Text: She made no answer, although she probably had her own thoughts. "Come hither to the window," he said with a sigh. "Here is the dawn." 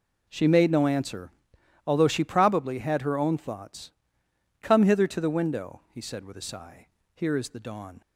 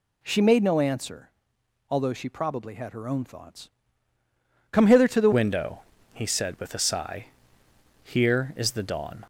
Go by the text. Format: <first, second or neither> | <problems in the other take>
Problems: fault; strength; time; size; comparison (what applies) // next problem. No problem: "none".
first | changes voice at "window"; from 5.3 s on; 3.9 s long